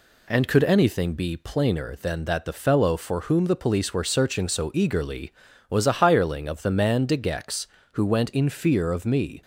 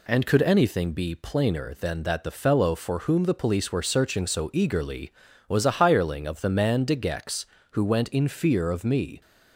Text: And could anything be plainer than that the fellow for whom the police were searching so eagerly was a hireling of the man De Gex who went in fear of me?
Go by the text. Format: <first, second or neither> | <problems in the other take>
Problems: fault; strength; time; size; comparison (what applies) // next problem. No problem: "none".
neither | none